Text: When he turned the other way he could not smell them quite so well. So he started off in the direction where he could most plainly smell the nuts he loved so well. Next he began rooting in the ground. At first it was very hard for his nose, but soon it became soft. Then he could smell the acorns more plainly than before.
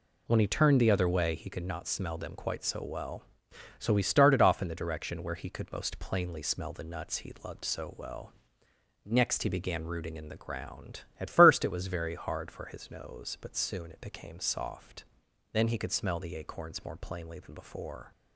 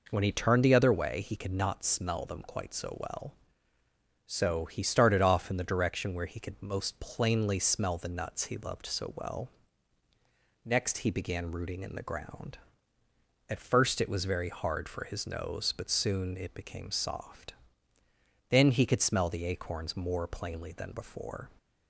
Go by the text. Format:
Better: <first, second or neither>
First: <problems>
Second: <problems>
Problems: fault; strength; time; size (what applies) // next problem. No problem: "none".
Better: neither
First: none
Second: none